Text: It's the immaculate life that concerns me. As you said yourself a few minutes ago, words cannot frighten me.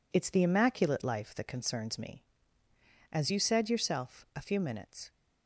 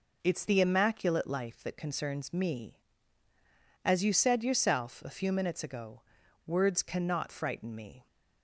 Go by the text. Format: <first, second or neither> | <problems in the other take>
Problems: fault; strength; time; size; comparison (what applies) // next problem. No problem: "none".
second | stops before "ago words cannot frighten me"; at 5.0 s